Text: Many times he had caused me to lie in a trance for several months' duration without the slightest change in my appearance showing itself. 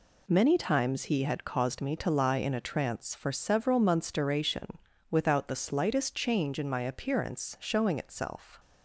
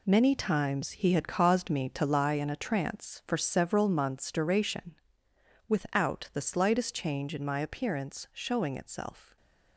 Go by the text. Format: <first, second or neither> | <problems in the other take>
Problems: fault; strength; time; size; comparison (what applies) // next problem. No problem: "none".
first | gets quieter; strong; throughout; 9.5 dB // pauses between "duration" and "without"; noticeable; at 4.9 s; 0.74 s long; slight in the first